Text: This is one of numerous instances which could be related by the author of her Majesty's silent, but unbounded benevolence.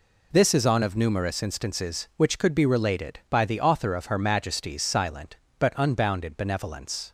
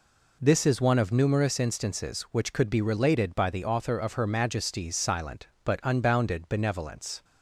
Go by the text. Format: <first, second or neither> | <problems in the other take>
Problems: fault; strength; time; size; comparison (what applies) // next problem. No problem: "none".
second | says "on" for "one"; at 0.6 s